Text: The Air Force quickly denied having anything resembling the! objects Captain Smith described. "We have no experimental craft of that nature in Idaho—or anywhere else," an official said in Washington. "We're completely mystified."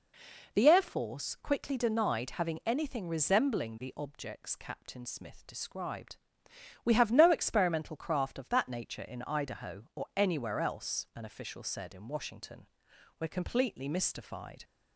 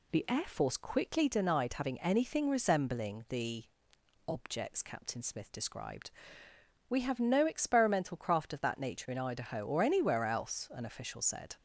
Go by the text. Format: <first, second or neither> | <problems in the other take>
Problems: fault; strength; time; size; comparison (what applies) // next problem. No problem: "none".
first | stops before "in Washington We're completely mystified"; at 11.5 s